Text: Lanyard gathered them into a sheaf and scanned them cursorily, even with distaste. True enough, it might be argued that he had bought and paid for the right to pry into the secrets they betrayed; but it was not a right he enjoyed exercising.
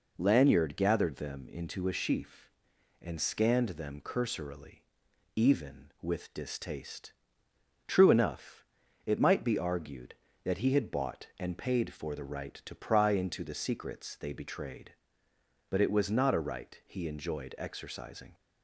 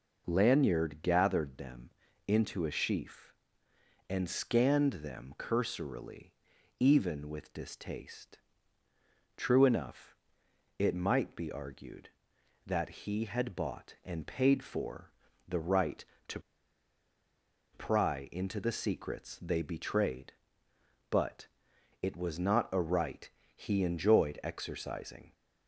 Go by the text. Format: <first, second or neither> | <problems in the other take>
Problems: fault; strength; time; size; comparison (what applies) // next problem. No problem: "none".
first | pauses between "them" and "into"; slight; at 1.8 s; 0.36 s long // pauses between "for" and "the"; slight; at 15.1 s; 0.36 s long // pauses between "to" and "pry"; strong; at 16.3 s; 1.3 s long // pauses between "but" and "it"; noticeable; at 21.4 s; 0.56 s long // pauses between "right" and "he"; slight; at 23.3 s; 0.24 s long